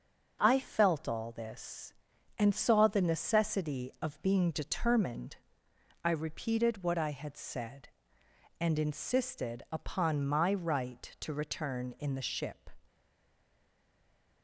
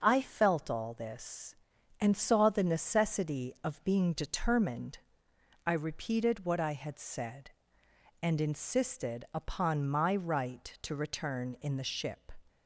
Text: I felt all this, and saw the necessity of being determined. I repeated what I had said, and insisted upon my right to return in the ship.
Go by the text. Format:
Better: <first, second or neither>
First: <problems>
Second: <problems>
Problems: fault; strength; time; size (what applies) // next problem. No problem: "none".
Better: second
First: starts louder than the rest; until 1.4 s; 6.5 dB // stays silent after the last word; noticeable; from 12.8 s on; 1.6 s long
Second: starts louder than the rest; until 1.0 s; 6.5 dB